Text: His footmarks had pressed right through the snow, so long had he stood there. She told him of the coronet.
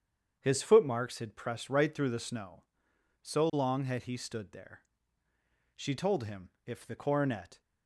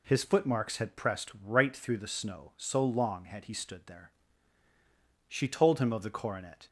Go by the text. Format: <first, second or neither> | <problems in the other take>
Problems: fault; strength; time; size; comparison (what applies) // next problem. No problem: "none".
second | starts louder than the rest; strong; until 1.4 s; 8 dB // says "if" for "of"; at 6.6 s